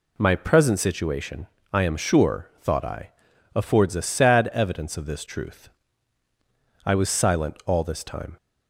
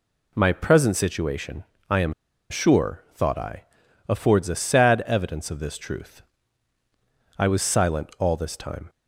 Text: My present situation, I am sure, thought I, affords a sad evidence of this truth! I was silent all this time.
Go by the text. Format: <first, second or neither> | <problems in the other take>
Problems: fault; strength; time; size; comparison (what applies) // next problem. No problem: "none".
first | pauses between "am" and "sure"; at 2.1 s; 0.37 s long